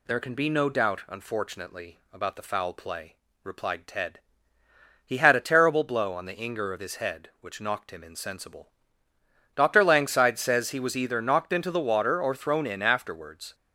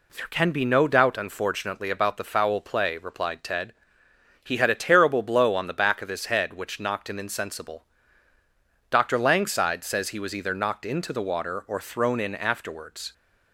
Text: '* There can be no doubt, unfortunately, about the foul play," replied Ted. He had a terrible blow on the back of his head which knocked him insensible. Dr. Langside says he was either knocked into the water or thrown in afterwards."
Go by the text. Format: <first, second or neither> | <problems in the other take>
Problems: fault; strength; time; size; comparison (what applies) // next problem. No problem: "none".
second | says "inger" for "back"; at 6.3 s